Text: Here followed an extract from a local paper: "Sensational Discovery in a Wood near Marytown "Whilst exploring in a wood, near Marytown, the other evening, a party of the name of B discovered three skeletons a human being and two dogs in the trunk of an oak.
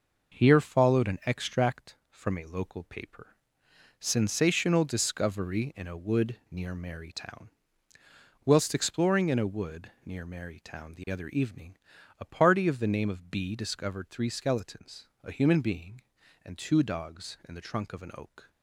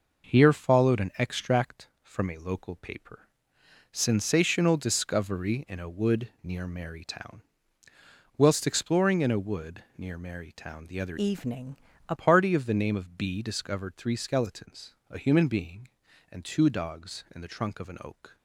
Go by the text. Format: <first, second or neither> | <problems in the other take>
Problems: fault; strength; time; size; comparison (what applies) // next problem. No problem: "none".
first | pauses between "Marytown" and "Whilst"; noticeable; at 7.4 s; 0.92 s long; noticeable in the first // changes voice from "evening" to "a"; from 11.1 to 12.1 s; 1.0 s long // pauses between "skeletons" and "a"; slight; at 14.9 s; 0.16 s long; slight in the first